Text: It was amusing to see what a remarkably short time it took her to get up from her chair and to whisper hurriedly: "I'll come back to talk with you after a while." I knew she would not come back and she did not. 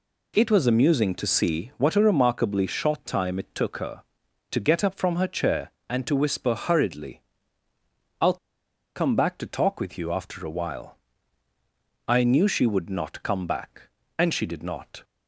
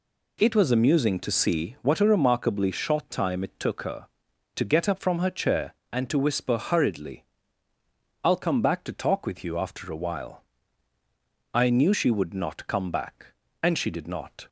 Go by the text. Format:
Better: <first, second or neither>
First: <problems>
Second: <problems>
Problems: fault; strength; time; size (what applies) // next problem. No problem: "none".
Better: second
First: pauses between "I'll" and "come"; noticeable; at 8.3 s; 0.59 s long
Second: none